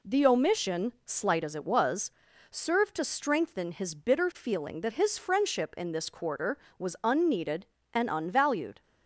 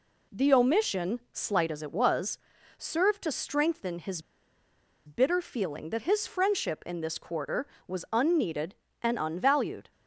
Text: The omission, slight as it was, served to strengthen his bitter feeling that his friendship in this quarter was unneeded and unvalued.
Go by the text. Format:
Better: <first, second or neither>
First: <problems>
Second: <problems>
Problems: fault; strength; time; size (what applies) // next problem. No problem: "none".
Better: first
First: none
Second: pauses between "his" and "bitter"; noticeable; at 4.2 s; 0.85 s long